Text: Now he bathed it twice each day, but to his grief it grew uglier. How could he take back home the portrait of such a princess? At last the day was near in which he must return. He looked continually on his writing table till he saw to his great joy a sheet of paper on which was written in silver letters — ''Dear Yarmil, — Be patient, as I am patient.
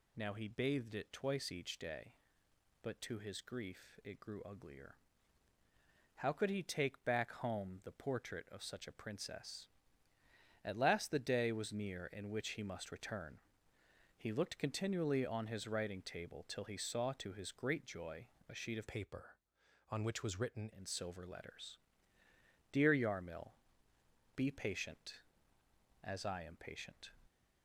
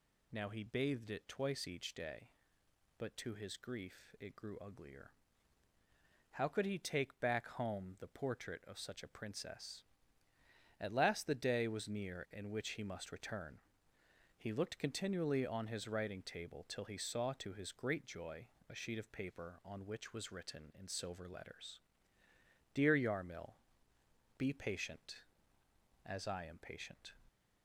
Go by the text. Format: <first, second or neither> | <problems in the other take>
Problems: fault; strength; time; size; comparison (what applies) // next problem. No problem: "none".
second | pauses between "joy" and "a"; slight; at 18.2 s; 0.22 s long; slight in the second // changes voice from "paper" to "written"; from 18.8 to 20.6 s; 1.8 s long